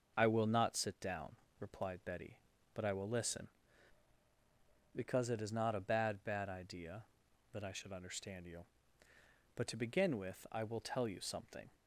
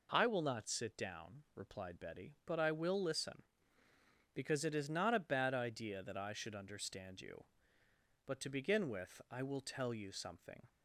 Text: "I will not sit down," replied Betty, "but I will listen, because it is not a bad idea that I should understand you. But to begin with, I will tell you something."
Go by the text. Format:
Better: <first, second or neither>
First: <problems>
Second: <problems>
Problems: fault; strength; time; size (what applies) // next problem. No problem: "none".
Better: second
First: starts louder than the rest; until 1.1 s; 6 dB // says "bad" twice; at 6.2 s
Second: none